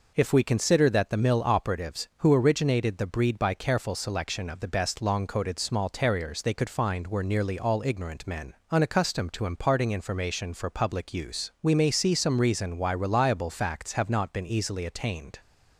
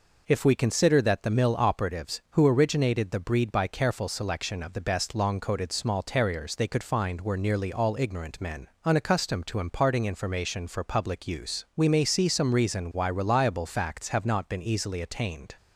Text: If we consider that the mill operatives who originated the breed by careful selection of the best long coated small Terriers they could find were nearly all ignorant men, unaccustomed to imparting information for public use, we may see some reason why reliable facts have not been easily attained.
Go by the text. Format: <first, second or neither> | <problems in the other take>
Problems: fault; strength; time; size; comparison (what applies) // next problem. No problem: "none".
neither | none